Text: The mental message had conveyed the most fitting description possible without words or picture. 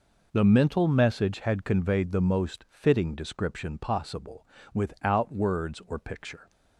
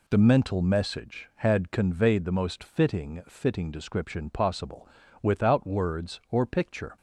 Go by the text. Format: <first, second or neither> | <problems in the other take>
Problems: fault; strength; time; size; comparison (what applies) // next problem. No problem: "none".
first | says "fitting" twice; at 3.2 s // pauses between "possible" and "without"; slight; at 4.8 s; 0.34 s long; slight in the first